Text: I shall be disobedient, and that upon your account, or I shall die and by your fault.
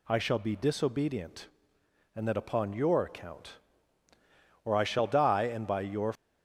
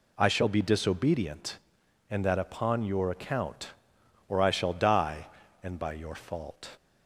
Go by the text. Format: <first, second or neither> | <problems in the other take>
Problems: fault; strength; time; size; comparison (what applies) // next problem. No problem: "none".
second | stops before "fault"; at 6.1 s